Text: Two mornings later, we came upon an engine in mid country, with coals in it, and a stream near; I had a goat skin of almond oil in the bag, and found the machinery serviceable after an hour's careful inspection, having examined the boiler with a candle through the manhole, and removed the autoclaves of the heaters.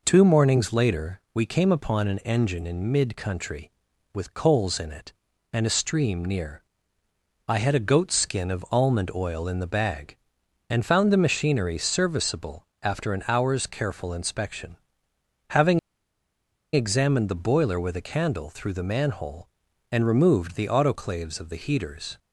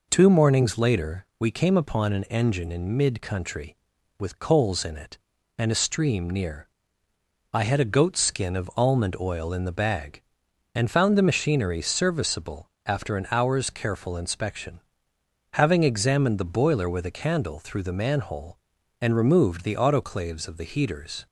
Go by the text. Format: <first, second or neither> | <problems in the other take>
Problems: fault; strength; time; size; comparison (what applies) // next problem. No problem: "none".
second | pauses between "serviceable" and "after"; slight; at 12.6 s; 0.16 s long; slight in the second // pauses between "having" and "examined"; noticeable; at 15.7 s; 0.94 s long